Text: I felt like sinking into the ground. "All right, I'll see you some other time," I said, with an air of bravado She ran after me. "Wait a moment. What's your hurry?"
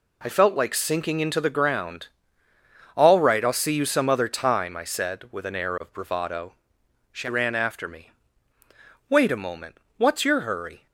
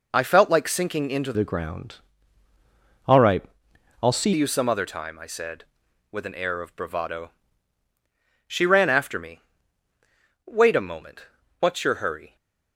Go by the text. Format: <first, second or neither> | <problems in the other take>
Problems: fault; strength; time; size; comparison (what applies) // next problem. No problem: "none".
first | changes voice from "the" to "see"; from 1.3 to 4.3 s; 3.0 s long // pauses between "bravado" and "She"; at 7.3 s; 1.1 s long; noticeable in the first